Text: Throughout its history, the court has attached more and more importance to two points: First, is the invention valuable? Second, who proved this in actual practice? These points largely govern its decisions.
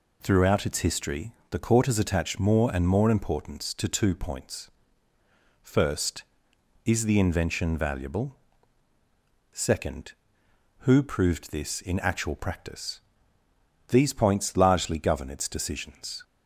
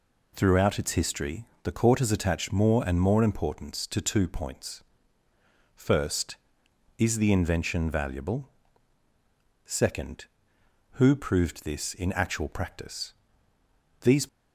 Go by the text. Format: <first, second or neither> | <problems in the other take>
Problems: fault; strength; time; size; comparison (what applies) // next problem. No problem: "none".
first | stops before "points largely govern its decisions"; at 14.2 s